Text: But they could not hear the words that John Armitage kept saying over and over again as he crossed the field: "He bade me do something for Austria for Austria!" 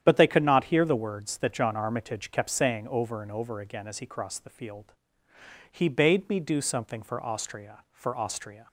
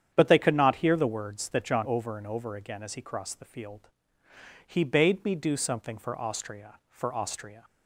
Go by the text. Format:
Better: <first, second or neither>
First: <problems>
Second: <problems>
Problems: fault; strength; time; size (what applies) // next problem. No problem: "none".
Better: first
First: starts louder than the rest; strong; until 1.0 s; 10 dB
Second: starts louder than the rest; strong; until 1.1 s; 9 dB // skips "Armitage kept saying"; at 1.8 s